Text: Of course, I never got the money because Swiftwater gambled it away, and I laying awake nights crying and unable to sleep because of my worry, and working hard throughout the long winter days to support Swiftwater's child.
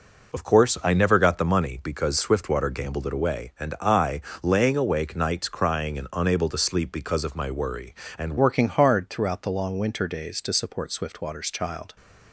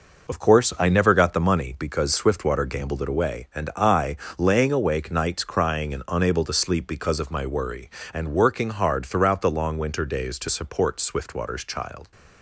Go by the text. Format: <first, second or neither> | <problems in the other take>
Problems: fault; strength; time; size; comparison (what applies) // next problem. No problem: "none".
second | pauses between "I" and "laying"; slight; at 4.1 s; 0.24 s long; slight in the second // changes voice at "working"; from 8.3 s on; 3.6 s long